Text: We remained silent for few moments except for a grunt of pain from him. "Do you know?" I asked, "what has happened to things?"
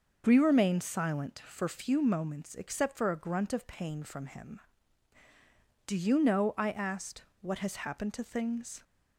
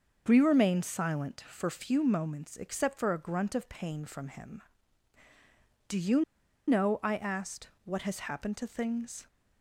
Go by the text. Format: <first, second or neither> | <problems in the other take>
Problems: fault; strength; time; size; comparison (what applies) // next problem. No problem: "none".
first | starts louder than the rest; until 1.2 s; 6 dB; noticeable in the first // pauses between "you" and "know"; at 6.2 s; 0.44 s long